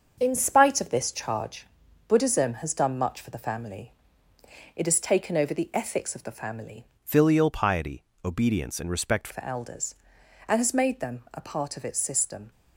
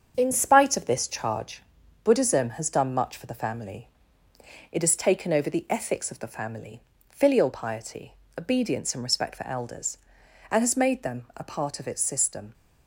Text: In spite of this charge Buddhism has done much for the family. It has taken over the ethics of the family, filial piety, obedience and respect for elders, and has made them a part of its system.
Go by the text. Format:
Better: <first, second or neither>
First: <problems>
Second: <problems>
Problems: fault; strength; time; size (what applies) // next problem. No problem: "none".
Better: second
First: starts louder than the rest; until 1.2 s; 7 dB // pauses between "charge" and "Buddhism"; at 1.6 s; 0.44 s long // changes voice from "filial" to "respect"; from 7.0 to 9.2 s; 2.2 s long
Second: starts louder than the rest; strong; until 1.1 s; 7.5 dB // pauses between "charge" and "Buddhism"; at 1.6 s; 0.44 s long